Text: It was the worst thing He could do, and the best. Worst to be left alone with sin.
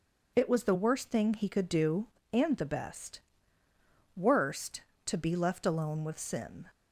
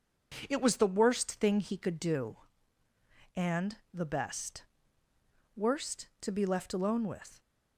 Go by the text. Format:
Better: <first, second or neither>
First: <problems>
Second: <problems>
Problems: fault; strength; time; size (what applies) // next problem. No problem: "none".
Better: first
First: none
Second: pauses between "and" and "the"; slight; at 3.7 s; 0.18 s long // stops before "sin"; at 7.4 s